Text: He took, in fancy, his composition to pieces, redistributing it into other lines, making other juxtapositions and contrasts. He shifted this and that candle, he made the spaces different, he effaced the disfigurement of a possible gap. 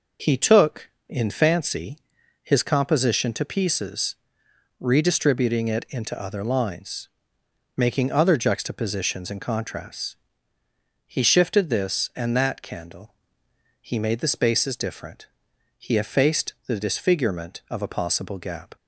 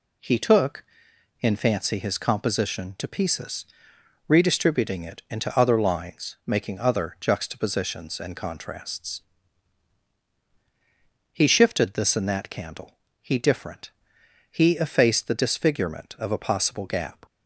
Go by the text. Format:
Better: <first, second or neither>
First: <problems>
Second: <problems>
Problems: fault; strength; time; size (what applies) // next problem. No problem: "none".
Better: first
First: none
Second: skips "made the spaces"; at 13.3 s